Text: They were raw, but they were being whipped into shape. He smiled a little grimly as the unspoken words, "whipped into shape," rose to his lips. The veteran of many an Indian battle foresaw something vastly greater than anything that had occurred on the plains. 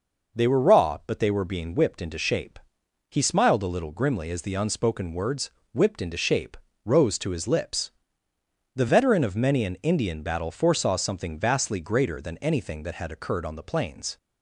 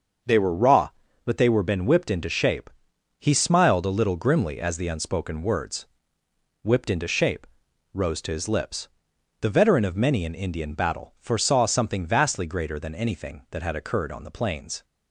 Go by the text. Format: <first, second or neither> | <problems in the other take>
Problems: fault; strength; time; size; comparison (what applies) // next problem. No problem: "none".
first | starts louder than the rest; until 1.6 s; 6.5 dB // says "been" for "being"; at 1.6 s